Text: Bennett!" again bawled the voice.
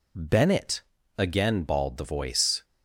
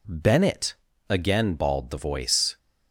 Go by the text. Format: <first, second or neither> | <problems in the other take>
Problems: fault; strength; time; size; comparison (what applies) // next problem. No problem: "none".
second | loses the start of "Bennett"; at 0.1 s; 30 ms